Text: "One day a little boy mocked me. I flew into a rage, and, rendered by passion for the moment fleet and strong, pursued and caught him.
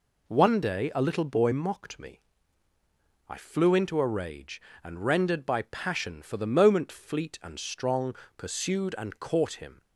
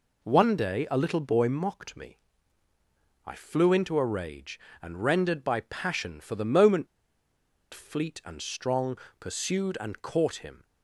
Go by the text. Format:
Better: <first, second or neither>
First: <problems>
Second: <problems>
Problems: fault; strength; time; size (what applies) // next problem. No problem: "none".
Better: first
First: none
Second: pauses between "moment" and "fleet"; noticeable; at 6.8 s; 0.86 s long